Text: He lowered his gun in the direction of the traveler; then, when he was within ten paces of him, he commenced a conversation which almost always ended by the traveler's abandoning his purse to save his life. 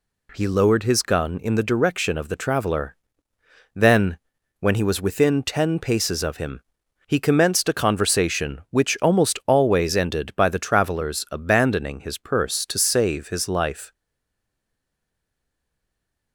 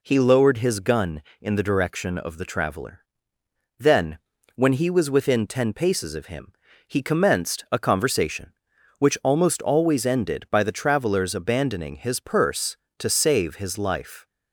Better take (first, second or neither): second